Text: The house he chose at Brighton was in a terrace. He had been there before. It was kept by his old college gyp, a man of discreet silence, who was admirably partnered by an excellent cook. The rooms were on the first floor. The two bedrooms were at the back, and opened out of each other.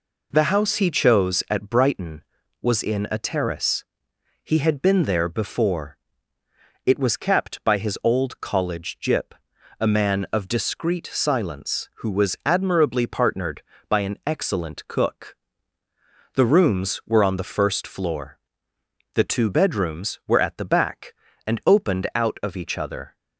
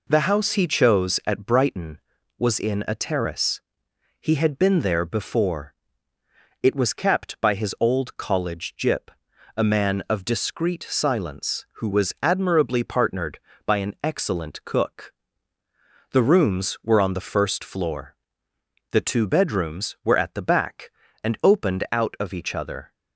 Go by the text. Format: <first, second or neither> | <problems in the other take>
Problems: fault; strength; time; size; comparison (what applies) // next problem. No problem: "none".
neither | none